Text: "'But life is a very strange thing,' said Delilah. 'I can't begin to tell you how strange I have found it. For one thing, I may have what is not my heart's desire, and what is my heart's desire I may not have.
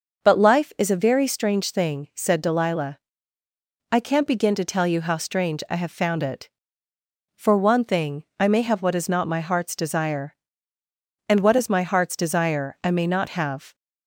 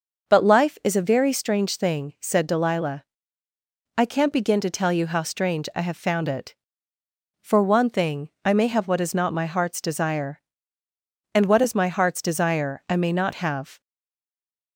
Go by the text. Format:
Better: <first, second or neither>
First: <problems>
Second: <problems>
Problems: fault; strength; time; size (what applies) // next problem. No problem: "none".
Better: first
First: starts louder than the rest; noticeable; until 1.2 s; 6 dB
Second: starts louder than the rest; noticeable; until 1.3 s; 6 dB // stays silent after the last word; from 13.8 s on; 0.9 s long